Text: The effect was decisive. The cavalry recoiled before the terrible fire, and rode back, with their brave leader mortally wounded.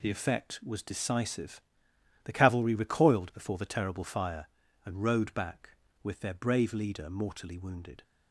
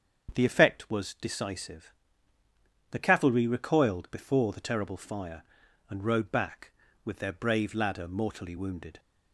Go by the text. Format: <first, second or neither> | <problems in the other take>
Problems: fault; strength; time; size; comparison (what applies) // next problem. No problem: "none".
first | starts louder than the rest; strong; until 1.3 s; 7.5 dB // says "ladder" for "leader"; at 7.7 s